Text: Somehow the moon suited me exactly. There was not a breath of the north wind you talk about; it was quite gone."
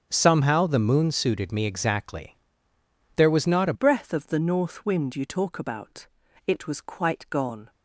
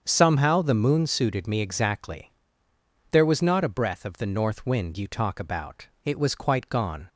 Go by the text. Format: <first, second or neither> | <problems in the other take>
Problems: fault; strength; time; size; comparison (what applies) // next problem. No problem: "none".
second | starts louder than the rest; strong; until 1.1 s; 8 dB; strong in the second // changes voice at "breath"; from 3.7 s on; 3.9 s long